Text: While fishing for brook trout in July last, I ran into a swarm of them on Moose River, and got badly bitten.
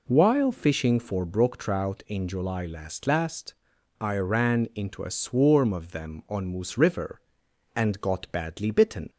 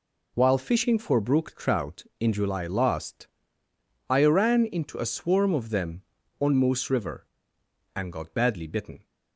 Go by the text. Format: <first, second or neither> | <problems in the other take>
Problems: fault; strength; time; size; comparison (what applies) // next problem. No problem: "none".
second | says "last" twice; at 3.0 s